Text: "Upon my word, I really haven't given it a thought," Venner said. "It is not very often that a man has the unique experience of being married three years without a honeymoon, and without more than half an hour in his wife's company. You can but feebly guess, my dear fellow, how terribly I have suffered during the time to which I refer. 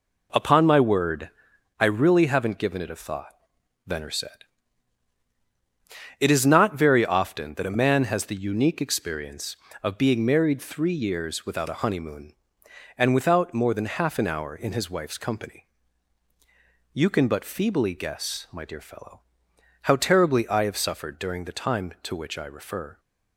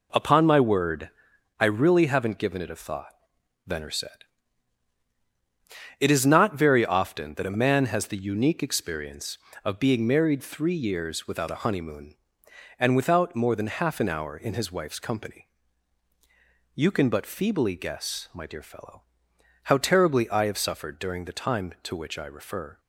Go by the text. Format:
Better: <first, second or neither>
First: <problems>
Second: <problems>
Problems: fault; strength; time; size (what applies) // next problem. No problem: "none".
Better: neither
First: none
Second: none